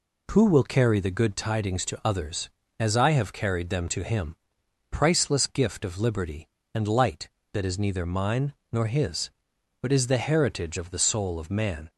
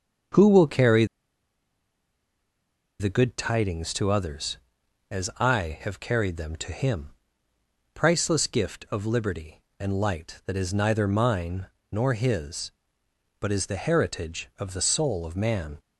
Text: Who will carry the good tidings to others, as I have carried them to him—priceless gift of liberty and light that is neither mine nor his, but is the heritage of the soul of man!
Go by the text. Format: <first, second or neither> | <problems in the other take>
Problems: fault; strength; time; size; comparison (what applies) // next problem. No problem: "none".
first | starts louder than the rest; until 3.2 s; 6.5 dB // pauses between "carry" and "the"; strong; at 1.0 s; 1.9 s long // pauses between "mine" and "nor"; slight; at 11.6 s; 0.24 s long; slight in the first